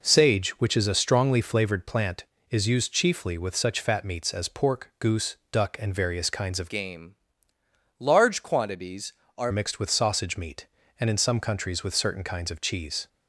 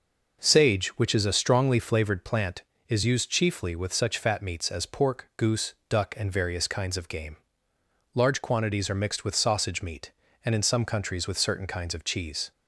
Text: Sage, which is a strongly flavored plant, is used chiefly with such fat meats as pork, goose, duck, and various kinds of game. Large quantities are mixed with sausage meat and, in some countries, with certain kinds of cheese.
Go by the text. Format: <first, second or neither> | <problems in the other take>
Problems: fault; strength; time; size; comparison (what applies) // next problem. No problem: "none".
second | changes voice from "game" to "are"; from 6.6 to 9.5 s; 2.9 s long